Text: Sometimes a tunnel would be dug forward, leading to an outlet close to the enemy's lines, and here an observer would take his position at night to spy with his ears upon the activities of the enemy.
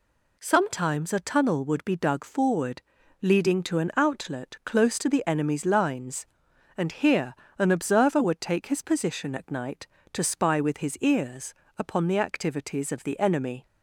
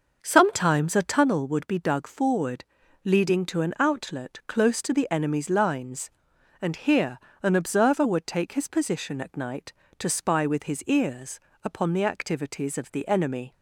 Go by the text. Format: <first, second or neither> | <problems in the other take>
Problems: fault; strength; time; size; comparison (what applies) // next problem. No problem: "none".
first | starts louder than the rest; until 1.3 s; 6 dB // pauses between "here" and "an"; slight; at 7.1 s; 0.24 s long; slight in the first // pauses between "ears" and "upon"; slight; at 11.4 s; 0.24 s long; slight in the first